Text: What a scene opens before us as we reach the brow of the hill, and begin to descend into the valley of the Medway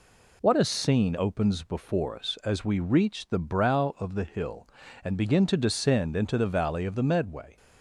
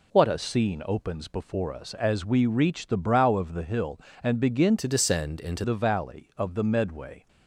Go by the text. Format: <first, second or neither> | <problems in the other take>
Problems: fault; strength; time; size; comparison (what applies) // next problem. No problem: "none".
first | changes voice from "to" to "into"; from 4.7 to 5.6 s; 0.9 s long